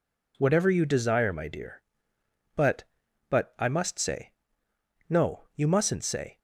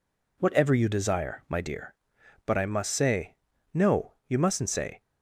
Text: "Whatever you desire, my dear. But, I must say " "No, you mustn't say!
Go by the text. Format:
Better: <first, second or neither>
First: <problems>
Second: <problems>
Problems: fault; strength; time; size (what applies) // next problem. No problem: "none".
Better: second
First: says "But" twice; at 3.2 s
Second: none